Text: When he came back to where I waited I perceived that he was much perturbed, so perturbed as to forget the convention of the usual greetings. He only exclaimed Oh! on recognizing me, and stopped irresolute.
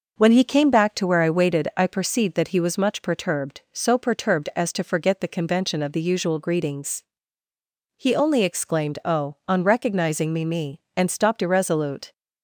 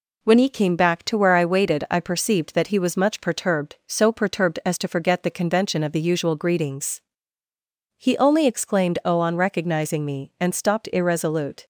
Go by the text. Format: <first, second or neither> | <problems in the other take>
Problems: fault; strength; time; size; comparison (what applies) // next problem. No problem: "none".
second | says "me" twice; at 10.4 s